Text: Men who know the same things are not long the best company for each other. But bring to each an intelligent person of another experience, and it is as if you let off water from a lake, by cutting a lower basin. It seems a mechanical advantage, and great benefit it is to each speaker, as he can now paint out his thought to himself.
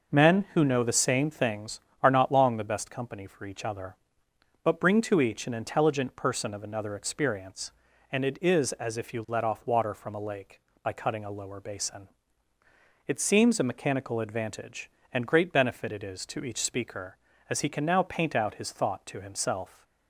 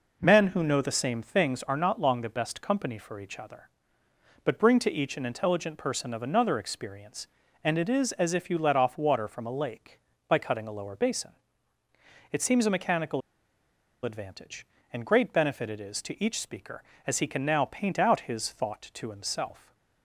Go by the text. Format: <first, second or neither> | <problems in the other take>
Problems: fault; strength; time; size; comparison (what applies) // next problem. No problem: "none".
first | pauses between "mechanical" and "advantage"; noticeable; at 13.2 s; 0.83 s long